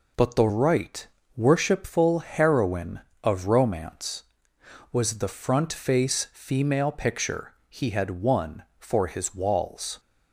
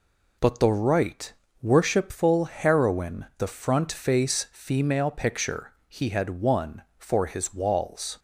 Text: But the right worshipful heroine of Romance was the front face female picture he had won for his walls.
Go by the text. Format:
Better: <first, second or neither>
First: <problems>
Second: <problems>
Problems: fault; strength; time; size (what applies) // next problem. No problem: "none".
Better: first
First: pauses between "right" and "worshipful"; slight; at 1.0 s; 0.28 s long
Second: pauses between "right" and "worshipful"; slight; at 1.3 s; 0.28 s long // skips "of Romance was"; at 3.3 s